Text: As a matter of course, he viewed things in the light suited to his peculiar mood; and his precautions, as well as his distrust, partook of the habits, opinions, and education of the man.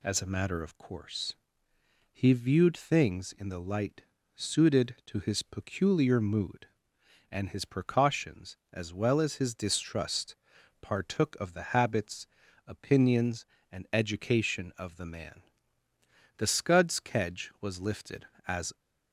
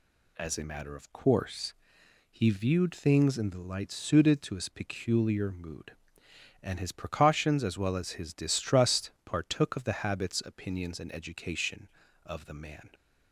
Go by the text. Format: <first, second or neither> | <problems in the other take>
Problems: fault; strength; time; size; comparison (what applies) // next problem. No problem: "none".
second | pauses between "light" and "suited"; slight; at 4.0 s; 0.32 s long // goes on to say "The Scud's kedge was lifted as"; strong; from 16.3 s on; 2.3 s long